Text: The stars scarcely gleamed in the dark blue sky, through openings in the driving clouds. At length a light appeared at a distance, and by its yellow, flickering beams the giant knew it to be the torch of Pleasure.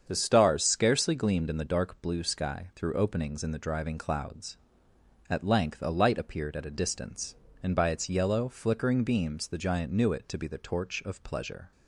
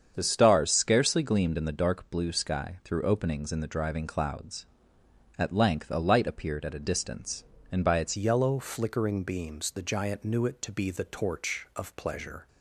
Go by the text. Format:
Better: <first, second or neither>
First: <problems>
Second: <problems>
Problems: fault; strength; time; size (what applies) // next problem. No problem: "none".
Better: first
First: starts louder than the rest; strong; until 1.0 s; 7.5 dB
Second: starts louder than the rest; strong; until 1.1 s; 7.5 dB // changes voice at "yellow"; from 8.1 s on; 4.3 s long